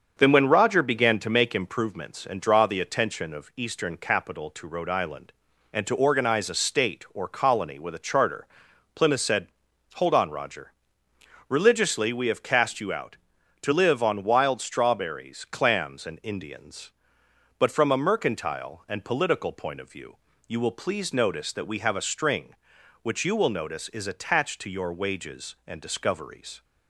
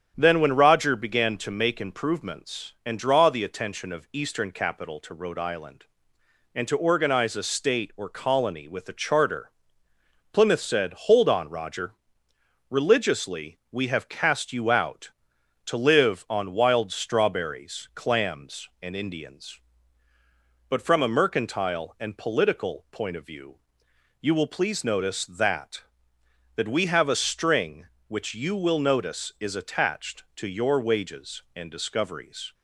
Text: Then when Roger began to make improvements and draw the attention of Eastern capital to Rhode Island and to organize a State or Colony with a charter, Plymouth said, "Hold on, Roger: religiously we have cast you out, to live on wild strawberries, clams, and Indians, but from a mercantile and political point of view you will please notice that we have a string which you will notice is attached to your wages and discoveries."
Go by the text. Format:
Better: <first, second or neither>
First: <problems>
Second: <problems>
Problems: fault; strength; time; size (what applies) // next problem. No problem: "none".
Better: first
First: starts louder than the rest; until 1.1 s; 7 dB // pauses between "view" and "you"; slight; at 20.1 s; 0.32 s long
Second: starts louder than the rest; strong; until 1.1 s; 9 dB // pauses between "view" and "you"; noticeable; at 23.5 s; 0.66 s long // says "that" twice; at 26.5 s